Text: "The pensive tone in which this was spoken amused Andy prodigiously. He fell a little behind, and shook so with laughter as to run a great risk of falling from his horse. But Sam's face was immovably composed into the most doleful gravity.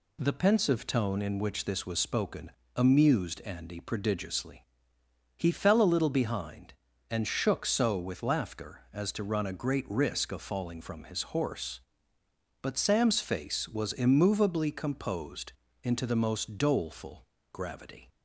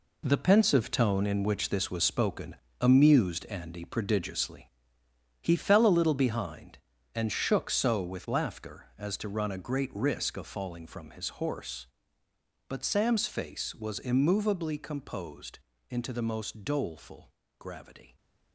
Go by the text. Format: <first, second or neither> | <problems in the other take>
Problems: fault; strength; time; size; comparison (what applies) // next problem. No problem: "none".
first | gets quieter; strong; throughout; 9 dB // pauses between "spoken" and "amused"; slight; at 2.5 s; 0.24 s long; slight in the first // pauses between "composed" and "into"; slight; at 15.5 s; 0.32 s long; slight in the first // pauses between "doleful" and "gravity"; slight; at 17.3 s; 0.28 s long; slight in the first